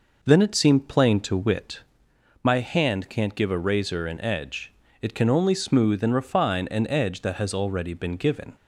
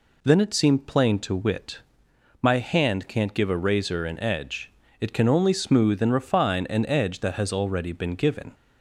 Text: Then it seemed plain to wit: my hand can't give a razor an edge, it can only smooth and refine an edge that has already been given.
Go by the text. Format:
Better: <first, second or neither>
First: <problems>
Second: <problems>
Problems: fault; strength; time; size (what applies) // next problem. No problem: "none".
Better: second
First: starts louder than the rest; noticeable; until 1.8 s; 5.5 dB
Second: none